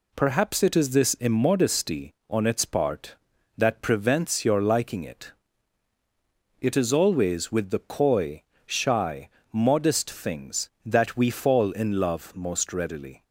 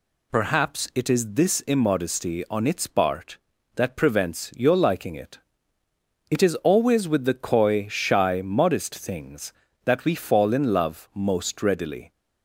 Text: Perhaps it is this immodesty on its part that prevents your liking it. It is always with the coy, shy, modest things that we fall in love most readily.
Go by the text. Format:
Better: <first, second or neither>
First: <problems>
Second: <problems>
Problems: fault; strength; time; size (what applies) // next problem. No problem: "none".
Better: neither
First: none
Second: none